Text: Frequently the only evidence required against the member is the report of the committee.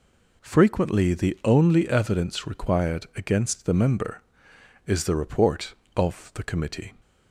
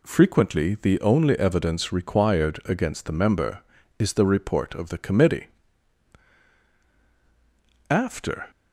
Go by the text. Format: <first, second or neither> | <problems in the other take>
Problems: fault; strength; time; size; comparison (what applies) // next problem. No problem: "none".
first | goes on to say "After"; from 7.9 s on; 0.60 s long